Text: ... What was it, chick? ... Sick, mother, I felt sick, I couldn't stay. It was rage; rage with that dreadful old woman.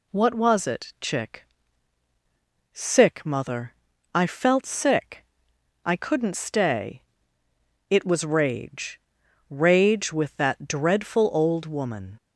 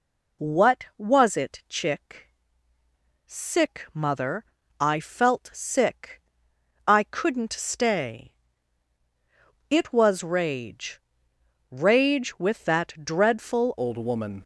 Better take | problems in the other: first | changes voice at "old"; from 13.7 s on; 0.7 s long

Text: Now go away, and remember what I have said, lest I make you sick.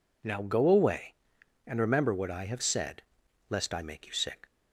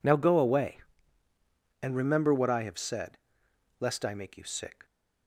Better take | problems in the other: neither | none

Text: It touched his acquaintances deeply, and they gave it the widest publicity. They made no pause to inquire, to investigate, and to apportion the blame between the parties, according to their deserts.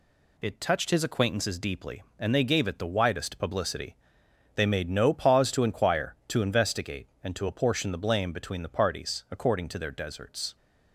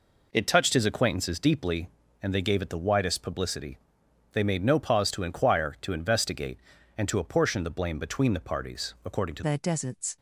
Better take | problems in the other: first | changes voice at "their"; from 9.4 s on; 0.7 s long

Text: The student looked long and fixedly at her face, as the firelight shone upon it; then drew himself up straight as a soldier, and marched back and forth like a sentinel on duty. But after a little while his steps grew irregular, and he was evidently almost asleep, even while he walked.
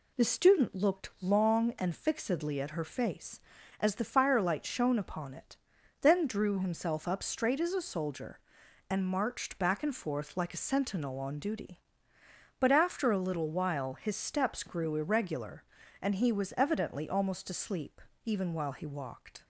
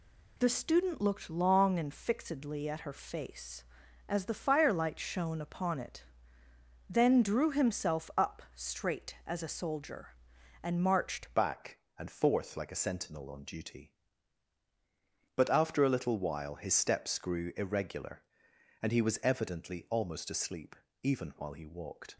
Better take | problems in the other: first | changes voice at "back"; from 11.3 s on; 10.8 s long

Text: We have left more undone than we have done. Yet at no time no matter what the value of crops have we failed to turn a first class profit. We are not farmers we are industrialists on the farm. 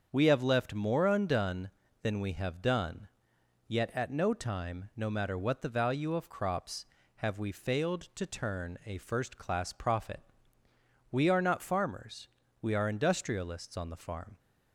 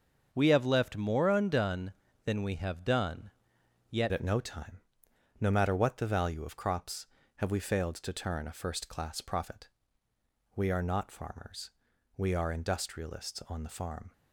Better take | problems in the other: first | starts louder than the rest; until 1.3 s; 6.5 dB; also in the first // changes voice at "at"; from 4.1 s on; 10.0 s long // pauses between "time" and "no"; noticeable; at 4.7 s; 0.62 s long // pauses between "farmers" and "we"; noticeable; at 11.7 s; 0.46 s long; slight in the first

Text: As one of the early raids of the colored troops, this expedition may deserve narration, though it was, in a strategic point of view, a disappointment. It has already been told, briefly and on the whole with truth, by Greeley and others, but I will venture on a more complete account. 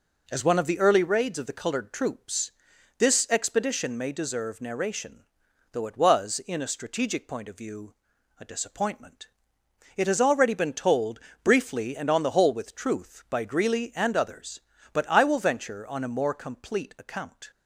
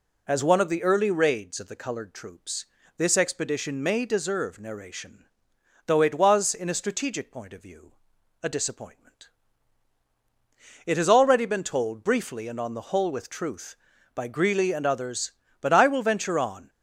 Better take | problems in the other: first | stops before "a more complete account"; at 16.6 s

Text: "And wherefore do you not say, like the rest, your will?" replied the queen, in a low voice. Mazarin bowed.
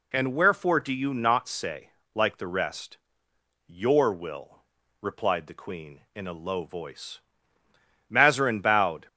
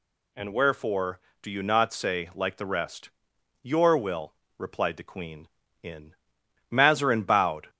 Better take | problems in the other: first | skips "a low voice"; at 6.4 s

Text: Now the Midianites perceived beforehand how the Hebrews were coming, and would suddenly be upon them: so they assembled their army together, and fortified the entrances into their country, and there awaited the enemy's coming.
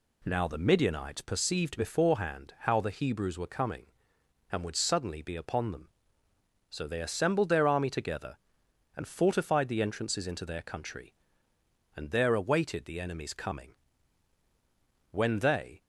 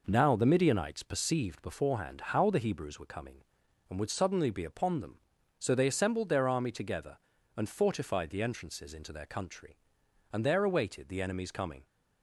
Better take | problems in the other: second | goes on to say "When they"; noticeable; from 15.1 s on; 0.70 s long

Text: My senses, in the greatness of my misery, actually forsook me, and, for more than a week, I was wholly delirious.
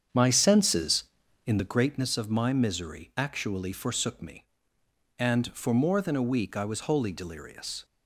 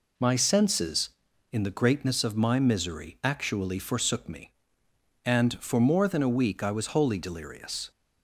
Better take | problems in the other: second | starts louder than the rest; strong; until 1.8 s; 8 dB

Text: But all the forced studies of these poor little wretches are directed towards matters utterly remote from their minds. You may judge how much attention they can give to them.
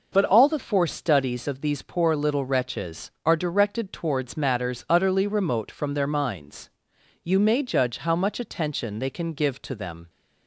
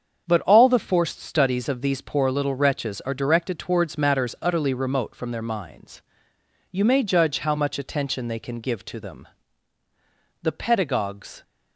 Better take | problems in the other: first | starts louder than the rest; until 1.2 s; 7 dB // goes on to say "The pedagogues"; noticeable; from 10.4 s on; 1.0 s long

